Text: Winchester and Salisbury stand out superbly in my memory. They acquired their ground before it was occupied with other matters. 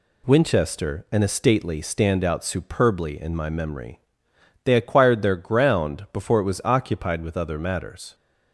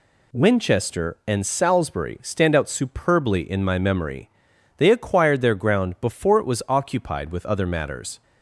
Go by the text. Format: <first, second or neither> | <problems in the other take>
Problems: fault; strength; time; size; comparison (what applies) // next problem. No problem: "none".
second | says "Estately" for "Salisbury"; at 1.2 s